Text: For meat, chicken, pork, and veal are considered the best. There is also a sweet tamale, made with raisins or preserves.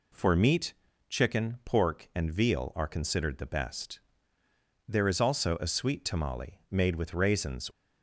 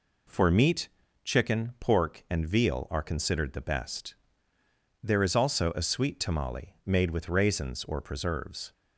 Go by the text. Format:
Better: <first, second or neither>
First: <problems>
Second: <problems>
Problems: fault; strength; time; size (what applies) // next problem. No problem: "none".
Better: second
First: stops before "or preserves"; at 7.7 s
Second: none